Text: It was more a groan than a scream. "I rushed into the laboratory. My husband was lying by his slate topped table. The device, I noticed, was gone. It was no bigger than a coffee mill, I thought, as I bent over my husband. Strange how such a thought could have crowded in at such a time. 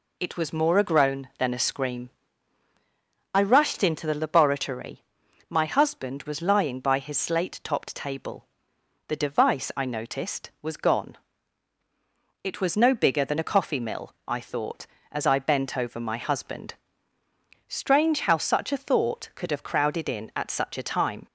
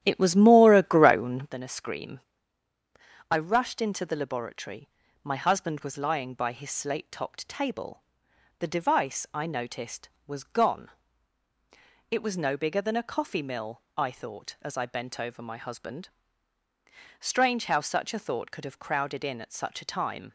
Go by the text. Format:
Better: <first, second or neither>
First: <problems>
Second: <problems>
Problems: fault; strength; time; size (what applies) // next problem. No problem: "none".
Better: first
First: none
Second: starts louder than the rest; strong; until 1.6 s; 11 dB